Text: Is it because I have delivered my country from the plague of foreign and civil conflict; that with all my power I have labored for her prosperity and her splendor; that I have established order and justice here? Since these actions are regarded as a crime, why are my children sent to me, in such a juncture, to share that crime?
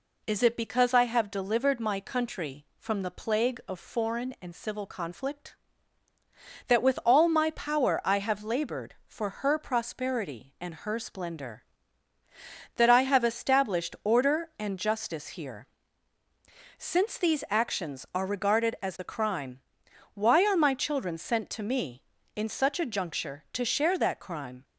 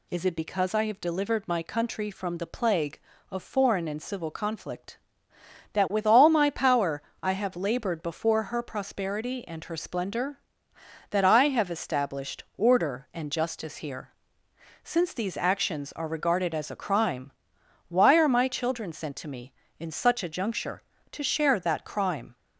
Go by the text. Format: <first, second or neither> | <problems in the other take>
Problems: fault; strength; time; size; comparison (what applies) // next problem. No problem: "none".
first | pauses between "power" and "I"; slight; at 6.9 s; 0.22 s long // says "before" for "for"; at 8.0 s // pauses between "established" and "order"; slight; at 12.4 s; 0.16 s long